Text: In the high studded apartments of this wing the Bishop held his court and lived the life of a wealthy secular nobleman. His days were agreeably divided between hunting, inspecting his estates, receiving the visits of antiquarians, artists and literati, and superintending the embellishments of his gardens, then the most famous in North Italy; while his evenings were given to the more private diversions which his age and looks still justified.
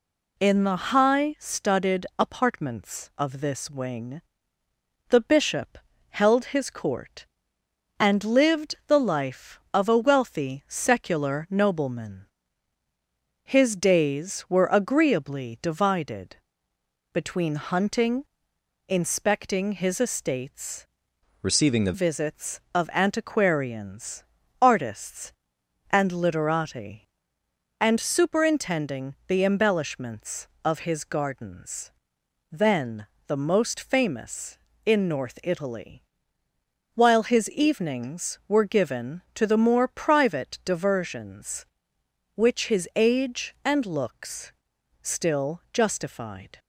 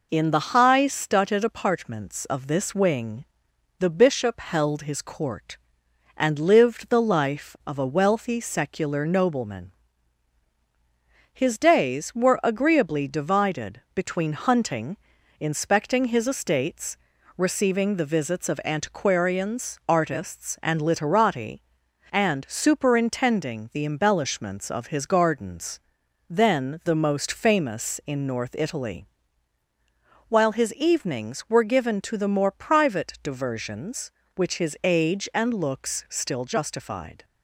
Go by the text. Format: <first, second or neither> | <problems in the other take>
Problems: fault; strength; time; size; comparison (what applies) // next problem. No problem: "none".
second | pauses between "wing" and "the"; noticeable; at 4.2 s; 0.88 s long; noticeable in the second // pauses between "Bishop" and "held"; slight; at 5.7 s; 0.30 s long // pauses between "divided" and "between"; noticeable; at 16.3 s; 0.76 s long // changes voice from "receiving" to "the"; from 21.3 to 21.9 s; 0.6 s long // pauses between "then" and "the"; slight; at 33.0 s; 0.20 s long // pauses between "looks" and "still"; noticeable; at 44.5 s; 0.48 s long